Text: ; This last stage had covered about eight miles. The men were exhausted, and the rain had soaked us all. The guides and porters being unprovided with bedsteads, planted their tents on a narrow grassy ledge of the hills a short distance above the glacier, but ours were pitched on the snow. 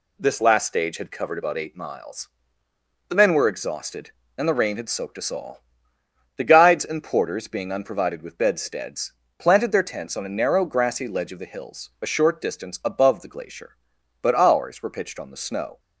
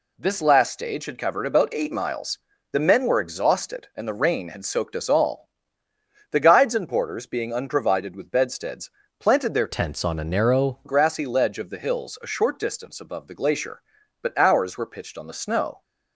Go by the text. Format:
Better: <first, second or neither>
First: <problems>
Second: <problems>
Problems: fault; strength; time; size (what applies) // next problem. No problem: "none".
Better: first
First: none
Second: changes voice from "tents" to "narrow"; from 9.6 to 10.7 s; 1.1 s long